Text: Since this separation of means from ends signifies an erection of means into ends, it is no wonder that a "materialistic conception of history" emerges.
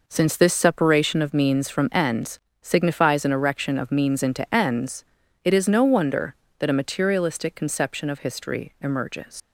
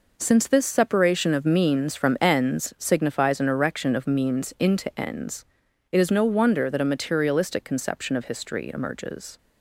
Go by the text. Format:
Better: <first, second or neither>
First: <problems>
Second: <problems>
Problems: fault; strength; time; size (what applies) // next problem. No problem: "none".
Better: second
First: pauses between "ends" and "signifies"; slight; at 2.3 s; 0.24 s long // leaves "emerges" unfinished; at 9.4 s; 95 ms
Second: none